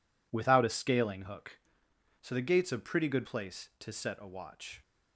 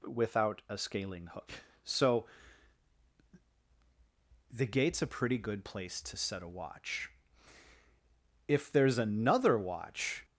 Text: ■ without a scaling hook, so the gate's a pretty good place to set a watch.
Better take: first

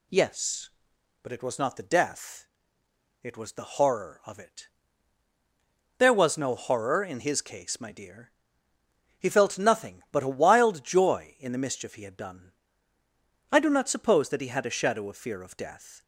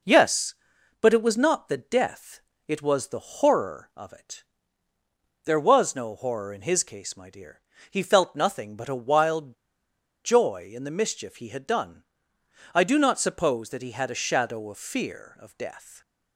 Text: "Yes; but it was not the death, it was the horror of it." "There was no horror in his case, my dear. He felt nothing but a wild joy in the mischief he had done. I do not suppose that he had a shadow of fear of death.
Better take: first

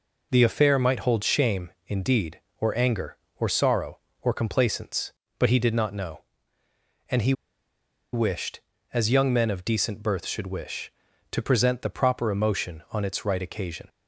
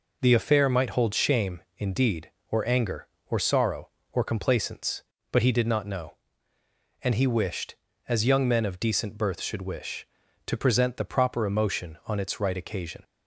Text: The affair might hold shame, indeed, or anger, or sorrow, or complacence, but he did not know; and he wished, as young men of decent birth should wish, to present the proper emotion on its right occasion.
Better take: second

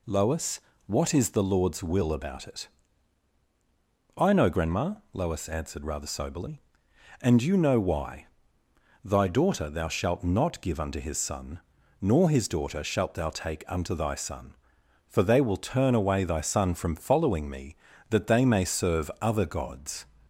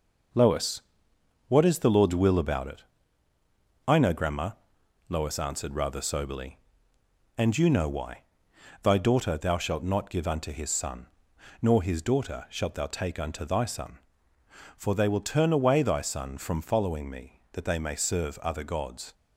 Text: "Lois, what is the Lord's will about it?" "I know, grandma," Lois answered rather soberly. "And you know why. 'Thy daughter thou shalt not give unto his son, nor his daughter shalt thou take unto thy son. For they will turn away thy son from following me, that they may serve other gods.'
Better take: first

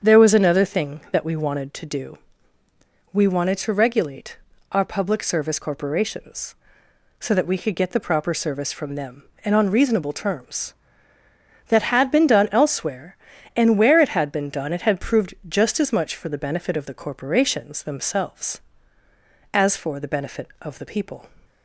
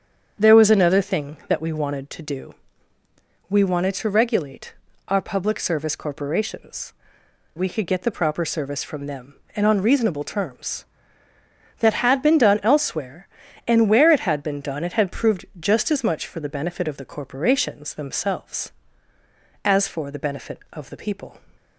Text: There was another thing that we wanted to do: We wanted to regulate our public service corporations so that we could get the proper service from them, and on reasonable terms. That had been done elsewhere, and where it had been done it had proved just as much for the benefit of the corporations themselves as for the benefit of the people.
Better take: first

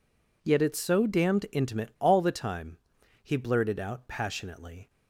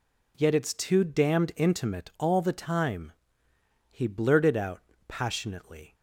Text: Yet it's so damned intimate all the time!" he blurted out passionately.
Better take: first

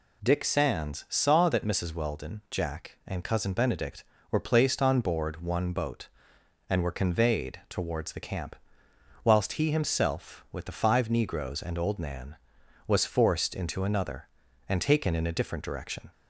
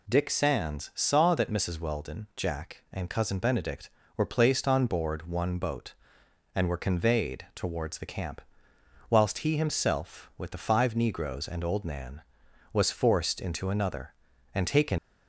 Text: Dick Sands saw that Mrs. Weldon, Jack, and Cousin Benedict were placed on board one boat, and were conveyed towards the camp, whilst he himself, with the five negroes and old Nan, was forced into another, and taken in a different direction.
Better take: first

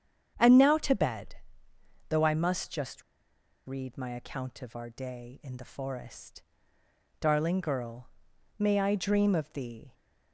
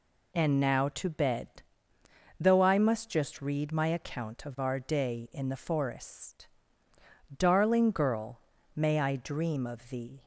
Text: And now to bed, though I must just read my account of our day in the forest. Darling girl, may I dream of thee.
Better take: second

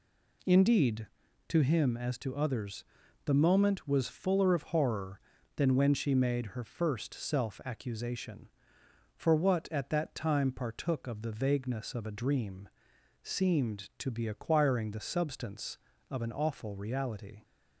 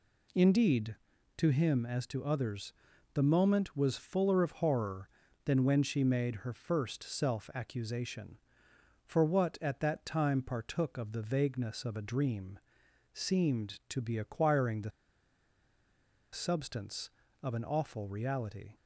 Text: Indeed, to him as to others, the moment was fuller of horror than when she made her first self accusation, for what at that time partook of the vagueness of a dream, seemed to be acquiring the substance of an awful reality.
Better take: first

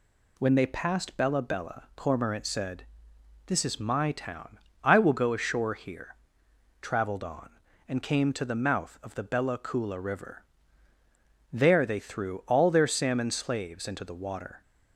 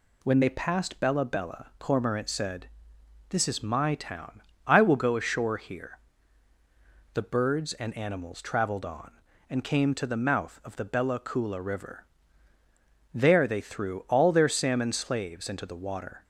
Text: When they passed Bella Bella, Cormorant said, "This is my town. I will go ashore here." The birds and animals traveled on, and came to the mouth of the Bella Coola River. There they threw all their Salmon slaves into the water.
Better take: second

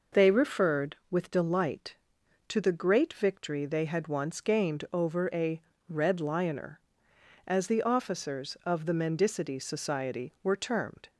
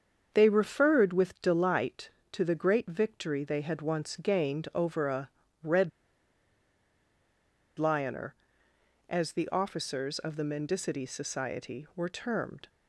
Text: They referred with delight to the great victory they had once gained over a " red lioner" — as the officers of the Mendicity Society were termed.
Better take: first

